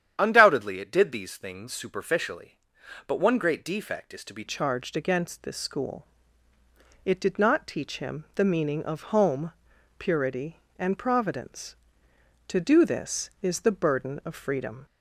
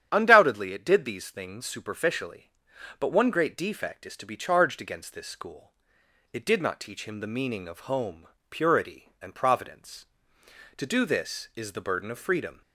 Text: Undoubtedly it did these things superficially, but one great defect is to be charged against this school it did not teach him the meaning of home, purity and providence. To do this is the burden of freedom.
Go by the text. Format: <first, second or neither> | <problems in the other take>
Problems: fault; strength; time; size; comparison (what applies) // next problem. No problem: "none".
second | starts louder than the rest; strong; until 1.1 s; 9.5 dB; strong in the second // changes voice at "charged"; from 4.4 s on; 10.4 s long // pauses between "school" and "it"; at 6.0 s; 1.0 s long; noticeable in the second